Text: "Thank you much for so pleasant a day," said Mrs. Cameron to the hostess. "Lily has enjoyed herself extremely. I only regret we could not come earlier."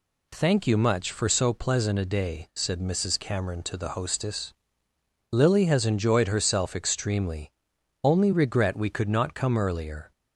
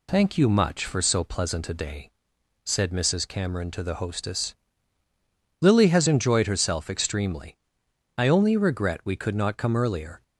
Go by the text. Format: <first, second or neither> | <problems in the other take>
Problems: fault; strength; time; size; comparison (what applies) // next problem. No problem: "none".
second | skips "I"; at 7.7 s